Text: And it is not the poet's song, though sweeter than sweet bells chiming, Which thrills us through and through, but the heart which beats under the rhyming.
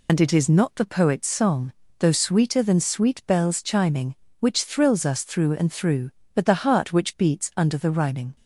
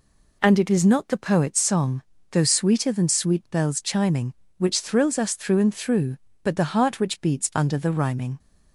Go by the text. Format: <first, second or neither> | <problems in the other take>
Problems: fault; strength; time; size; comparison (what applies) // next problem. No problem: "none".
second | loses the start of "And"; at 0.0 s; 65 ms